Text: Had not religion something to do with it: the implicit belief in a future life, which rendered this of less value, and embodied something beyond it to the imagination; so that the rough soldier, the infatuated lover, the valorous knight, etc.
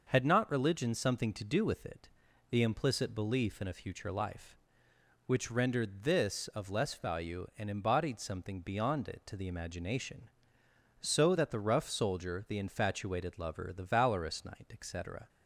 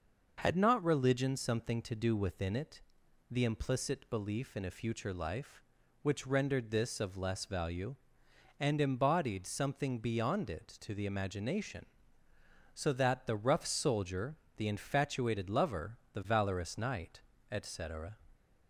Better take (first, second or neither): first